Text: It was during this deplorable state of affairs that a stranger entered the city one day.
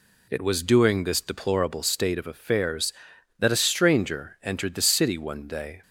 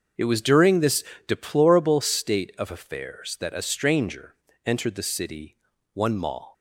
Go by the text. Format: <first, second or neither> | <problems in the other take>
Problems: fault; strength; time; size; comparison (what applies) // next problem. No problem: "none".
first | starts louder than the rest; until 1.4 s; 6.5 dB // pauses between "this" and "deplorable"; slight; at 1.0 s; 0.24 s long // pauses between "stranger" and "entered"; slight; at 4.3 s; 0.32 s long // pauses between "city" and "one"; at 5.5 s; 0.38 s long // says "mall" for "day"; at 6.1 s